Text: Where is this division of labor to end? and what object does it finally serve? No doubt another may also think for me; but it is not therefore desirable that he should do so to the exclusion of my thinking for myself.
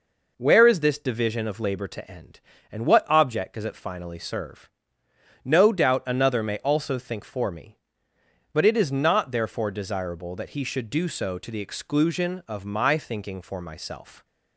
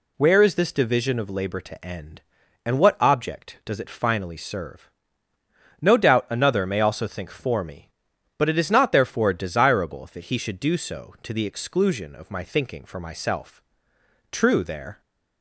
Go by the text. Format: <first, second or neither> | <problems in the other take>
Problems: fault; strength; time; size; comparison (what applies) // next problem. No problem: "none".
first | goes on to say "True there"; noticeable; from 14.3 s on; 0.70 s long